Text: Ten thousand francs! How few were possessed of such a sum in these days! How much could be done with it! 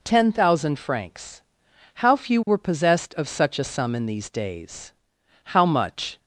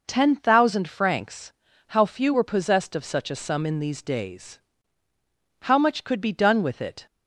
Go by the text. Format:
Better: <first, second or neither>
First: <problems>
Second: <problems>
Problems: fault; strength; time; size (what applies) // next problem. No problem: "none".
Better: second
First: stops before "could be done with it"; at 6.1 s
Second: none